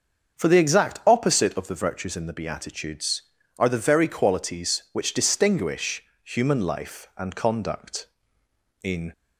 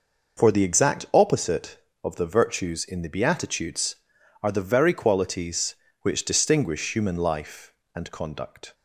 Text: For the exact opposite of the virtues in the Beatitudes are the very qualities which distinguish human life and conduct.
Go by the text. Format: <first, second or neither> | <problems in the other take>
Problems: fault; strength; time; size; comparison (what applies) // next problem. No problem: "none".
second | starts louder than the rest; until 1.4 s; 6.5 dB // pauses between "distinguish" and "human"; slight; at 6.0 s; 0.22 s long // goes on to say "In"; slight; from 8.8 s on; 0.30 s long